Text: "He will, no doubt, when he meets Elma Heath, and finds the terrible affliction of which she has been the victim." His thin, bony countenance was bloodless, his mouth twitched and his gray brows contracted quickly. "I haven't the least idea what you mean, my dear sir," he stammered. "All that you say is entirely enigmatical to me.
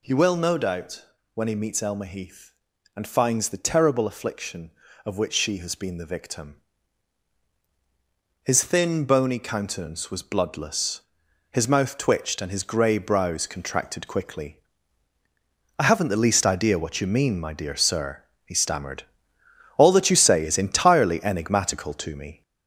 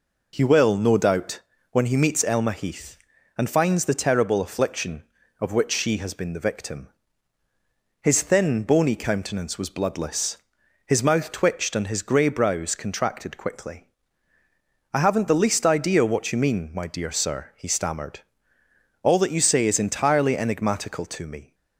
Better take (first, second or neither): second